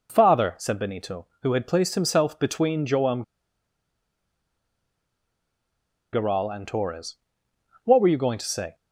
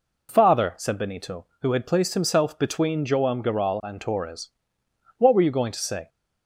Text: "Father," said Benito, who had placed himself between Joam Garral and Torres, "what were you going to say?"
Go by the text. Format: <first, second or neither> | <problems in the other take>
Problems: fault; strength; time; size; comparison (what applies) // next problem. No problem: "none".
second | pauses between "Joam" and "Garral"; strong; at 3.2 s; 2.9 s long